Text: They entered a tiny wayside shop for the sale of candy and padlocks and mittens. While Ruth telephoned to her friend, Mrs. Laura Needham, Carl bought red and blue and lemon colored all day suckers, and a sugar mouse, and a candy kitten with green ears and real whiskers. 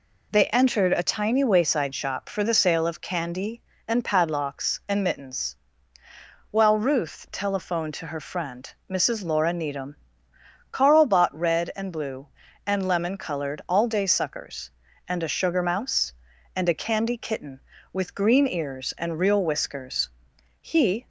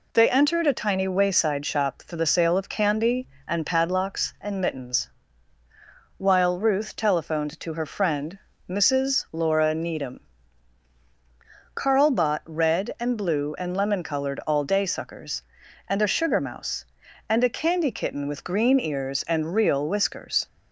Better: second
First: goes on to say "He"; slight; from 20.6 s on; 0.46 s long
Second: none

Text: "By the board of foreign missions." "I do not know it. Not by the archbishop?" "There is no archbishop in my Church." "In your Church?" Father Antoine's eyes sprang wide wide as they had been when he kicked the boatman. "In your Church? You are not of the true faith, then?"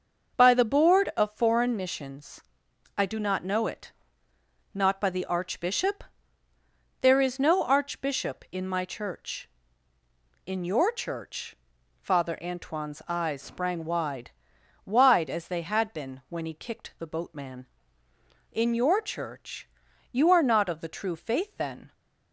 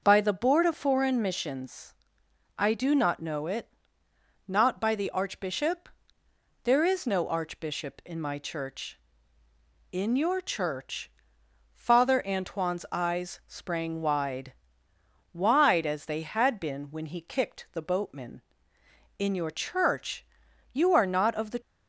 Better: first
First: pauses between "wide" and "wide"; noticeable; at 14.2 s; 0.56 s long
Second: starts louder than the rest; noticeable; until 1.0 s; 6 dB // pauses between "wide" and "wide"; noticeable; at 14.5 s; 0.80 s long // stops before "true faith then"; at 21.6 s

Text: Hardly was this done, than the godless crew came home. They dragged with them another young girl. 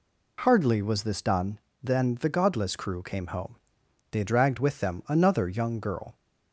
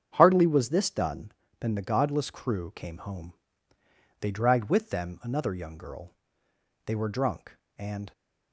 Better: first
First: none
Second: starts louder than the rest; strong; until 1.1 s; 8 dB // goes on to say "They were drunk and"; noticeable; from 6.8 s on; 1.2 s long

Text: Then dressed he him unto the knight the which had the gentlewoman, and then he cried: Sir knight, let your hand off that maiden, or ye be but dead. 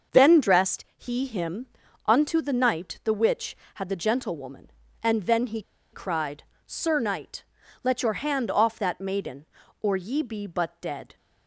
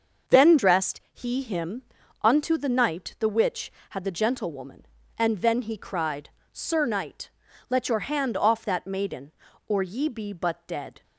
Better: second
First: starts louder than the rest; until 1.2 s; 6.5 dB // pauses between "him" and "unto"; at 1.6 s; 0.40 s long // pauses between "he" and "cried"; slight; at 5.6 s; 0.31 s long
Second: starts louder than the rest; until 1.4 s; 6.5 dB // pauses between "him" and "unto"; at 1.8 s; 0.40 s long

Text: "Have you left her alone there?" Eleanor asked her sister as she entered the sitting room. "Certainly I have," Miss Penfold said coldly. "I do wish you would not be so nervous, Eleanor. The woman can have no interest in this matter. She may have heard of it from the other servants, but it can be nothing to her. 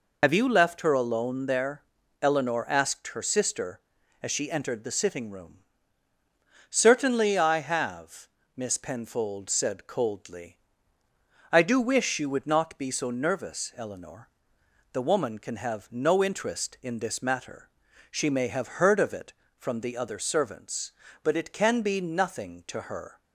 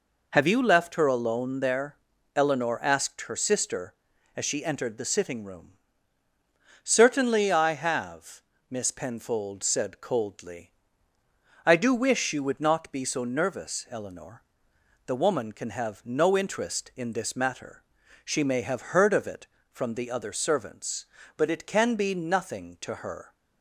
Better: second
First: loses the start of "Have"; at 0.2 s; 45 ms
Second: none

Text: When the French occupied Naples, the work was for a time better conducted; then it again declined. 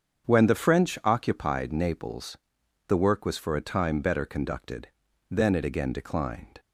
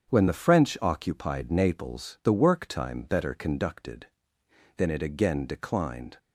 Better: first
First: starts louder than the rest; strong; until 1.3 s; 8 dB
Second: starts louder than the rest; strong; until 1.1 s; 7.5 dB // skips "was for a"; at 2.6 s

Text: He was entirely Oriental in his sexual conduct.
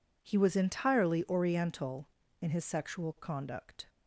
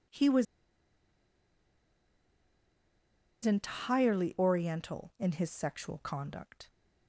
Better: first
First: none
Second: pauses between "was" and "entirely"; strong; at 0.4 s; 3.0 s long

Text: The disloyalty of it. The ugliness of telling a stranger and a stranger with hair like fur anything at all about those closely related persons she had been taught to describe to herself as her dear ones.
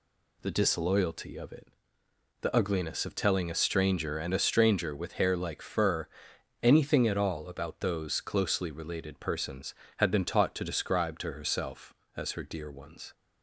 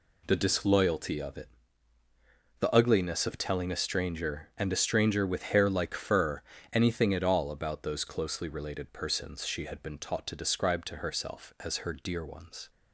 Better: second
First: pauses between "fur" and "anything"; noticeable; at 6.0 s; 0.56 s long // skips "she"; at 9.8 s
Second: pauses between "fur" and "anything"; slight; at 6.4 s; 0.32 s long

